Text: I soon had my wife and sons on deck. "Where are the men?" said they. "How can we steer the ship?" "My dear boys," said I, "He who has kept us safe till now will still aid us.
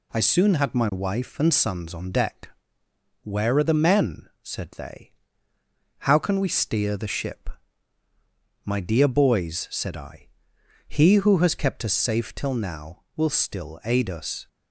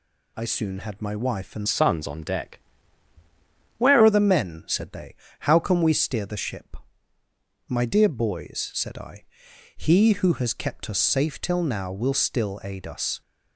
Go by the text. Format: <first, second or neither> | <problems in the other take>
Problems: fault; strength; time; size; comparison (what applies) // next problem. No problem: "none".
first | changes voice from "sons" to "Where"; from 1.6 to 4.0 s; 2.4 s long